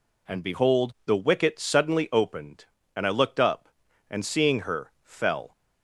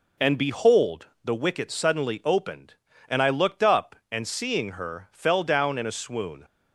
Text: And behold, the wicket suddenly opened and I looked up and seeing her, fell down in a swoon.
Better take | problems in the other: second | stops before "down in a swoon"; at 5.5 s

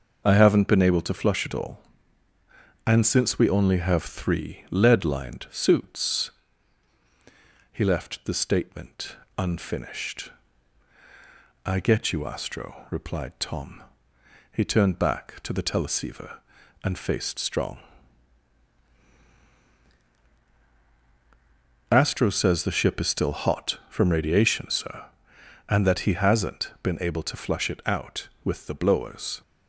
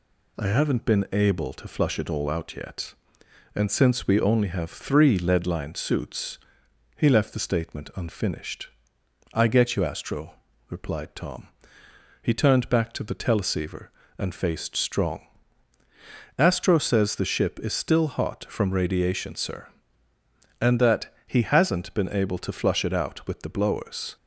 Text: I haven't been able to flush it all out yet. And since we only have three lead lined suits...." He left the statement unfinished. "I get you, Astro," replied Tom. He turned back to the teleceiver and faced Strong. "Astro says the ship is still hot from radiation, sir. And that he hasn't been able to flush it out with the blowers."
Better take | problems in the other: second | skips "out yet"; at 2.3 s // pauses between "statement" and "unfinished"; slight; at 9.1 s; 0.20 s long

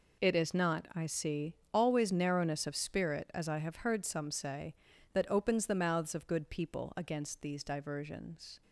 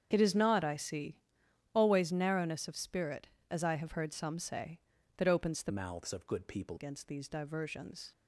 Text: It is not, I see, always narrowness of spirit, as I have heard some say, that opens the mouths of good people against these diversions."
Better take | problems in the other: first | starts louder than the rest; strong; until 1.1 s; 7.5 dB // changes voice from "mouths" to "people"; from 5.6 to 6.7 s; 1.1 s long

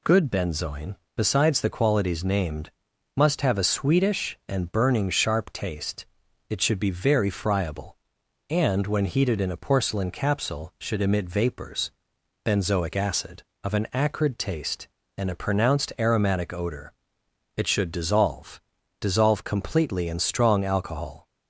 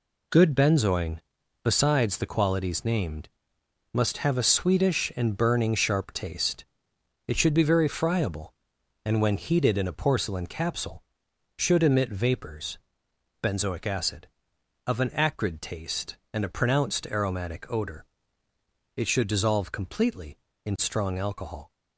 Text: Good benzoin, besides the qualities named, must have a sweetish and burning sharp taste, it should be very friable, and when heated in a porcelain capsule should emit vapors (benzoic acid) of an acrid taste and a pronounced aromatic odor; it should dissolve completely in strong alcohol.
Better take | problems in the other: second | says "dissolve" twice; at 18.9 s

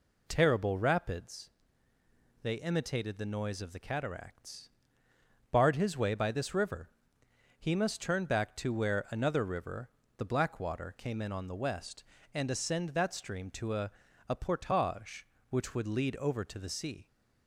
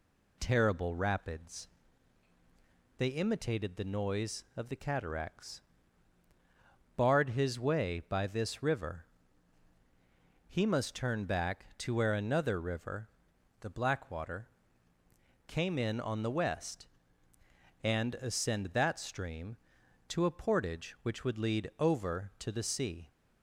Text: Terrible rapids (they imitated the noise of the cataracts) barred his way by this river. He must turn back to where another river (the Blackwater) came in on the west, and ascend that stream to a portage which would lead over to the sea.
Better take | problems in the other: second | says "a" twice; at 14.2 s

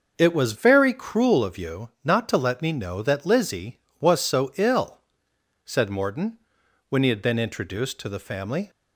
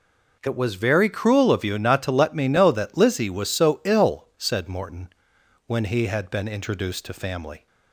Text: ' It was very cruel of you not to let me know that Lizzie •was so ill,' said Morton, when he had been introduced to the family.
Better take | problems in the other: first | skips "the"; at 7.1 s

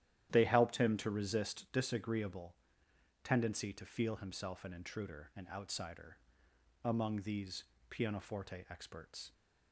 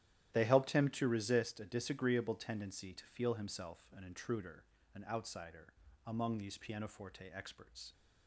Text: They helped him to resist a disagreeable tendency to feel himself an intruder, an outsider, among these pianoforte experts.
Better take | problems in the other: second | starts louder than the rest; strong; until 1.3 s; 12 dB; strong in the second // skips "a"; at 1.6 s // pauses between "disagreeable" and "tendency"; noticeable; at 2.5 s; 0.68 s long // pauses between "these" and "pianoforte"; slight; at 7.6 s; 0.24 s long

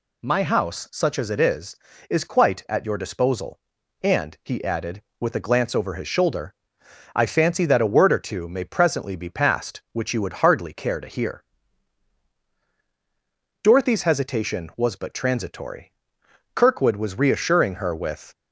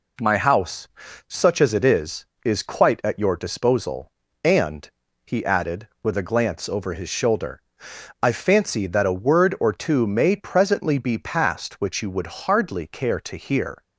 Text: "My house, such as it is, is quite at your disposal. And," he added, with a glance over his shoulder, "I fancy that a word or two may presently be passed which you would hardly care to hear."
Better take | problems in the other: second | goes on to say "Dorothy's hesitation was but transitory Kirkwood was reassuring her with"; strong; from 13.6 s on; 4.7 s long

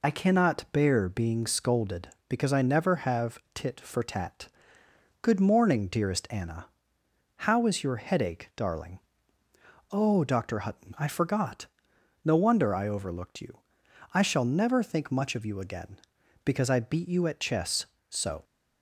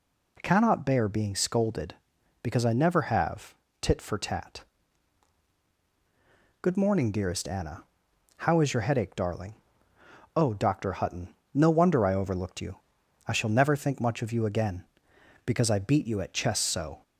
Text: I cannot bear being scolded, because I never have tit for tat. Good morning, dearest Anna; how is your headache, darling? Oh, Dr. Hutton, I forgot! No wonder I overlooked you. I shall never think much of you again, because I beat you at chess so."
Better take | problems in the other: first | pauses between "have" and "tit"; slight; at 3.5 s; 0.26 s long; slight in the first // skips "I forgot"; at 11.4 s

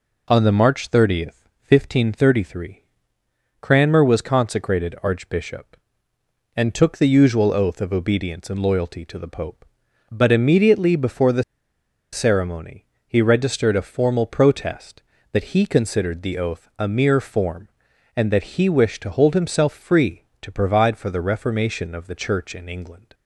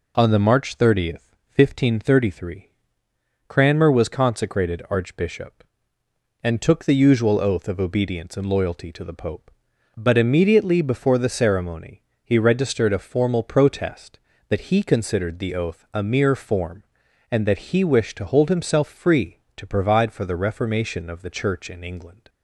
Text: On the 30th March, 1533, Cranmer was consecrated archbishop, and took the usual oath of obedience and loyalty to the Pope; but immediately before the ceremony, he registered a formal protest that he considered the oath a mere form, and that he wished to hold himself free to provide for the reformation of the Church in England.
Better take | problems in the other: second | pauses between "the" and "ceremony"; noticeable; at 11.4 s; 0.69 s long

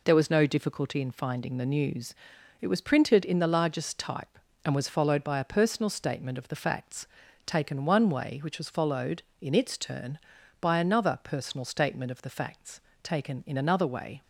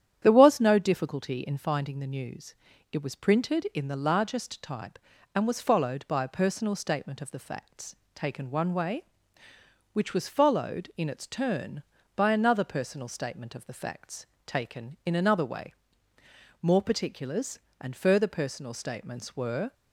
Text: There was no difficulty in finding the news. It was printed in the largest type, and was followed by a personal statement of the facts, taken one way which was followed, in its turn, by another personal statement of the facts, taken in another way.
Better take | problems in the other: first | starts louder than the rest; strong; until 1.2 s; 10 dB // goes on to say "More particulars and further personal statements were"; strong; from 16.6 s on; 3.1 s long

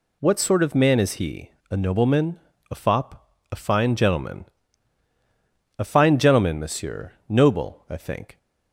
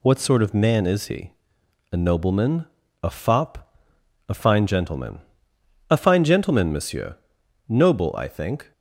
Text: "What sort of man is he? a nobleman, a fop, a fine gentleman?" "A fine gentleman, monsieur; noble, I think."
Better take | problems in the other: neither | none

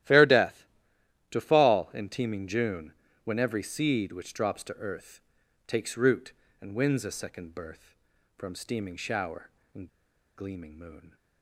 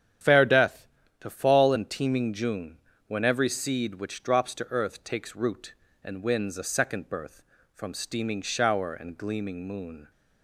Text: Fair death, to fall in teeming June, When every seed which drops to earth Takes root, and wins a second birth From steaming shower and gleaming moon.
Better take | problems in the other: second | starts louder than the rest; strong; until 1.6 s; 13.5 dB; strong in the second // pauses between "earth" and "Takes"; at 5.2 s; 0.44 s long // pauses between "and" and "gleaming"; noticeable; at 9.8 s; 0.49 s long

